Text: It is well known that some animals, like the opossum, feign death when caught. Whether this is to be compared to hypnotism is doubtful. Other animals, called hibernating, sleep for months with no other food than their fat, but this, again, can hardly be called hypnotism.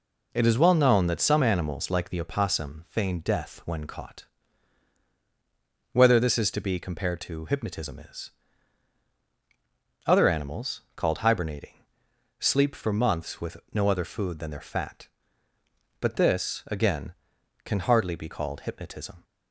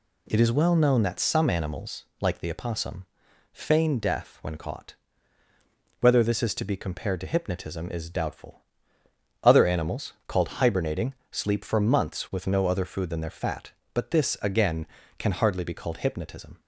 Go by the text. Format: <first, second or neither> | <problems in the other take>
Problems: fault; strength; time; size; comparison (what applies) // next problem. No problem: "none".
second | skips "doubtful"; at 9.1 s // pauses between "with" and "no"; slight; at 13.5 s; 0.16 s long